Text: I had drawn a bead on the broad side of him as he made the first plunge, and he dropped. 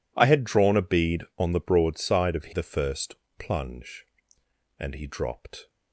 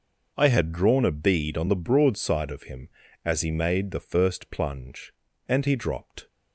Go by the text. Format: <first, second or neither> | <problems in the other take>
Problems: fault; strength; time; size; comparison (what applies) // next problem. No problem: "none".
second | skips "him as he made"; at 2.5 s // pauses between "first" and "plunge"; slight; at 3.1 s; 0.24 s long